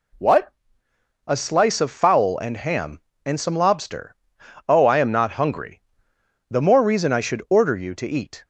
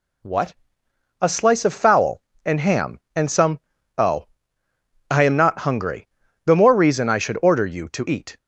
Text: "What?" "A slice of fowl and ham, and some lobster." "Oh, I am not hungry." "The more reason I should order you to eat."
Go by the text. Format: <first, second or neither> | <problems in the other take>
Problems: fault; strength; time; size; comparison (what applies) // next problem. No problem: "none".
first | skips "lobster"; at 3.7 s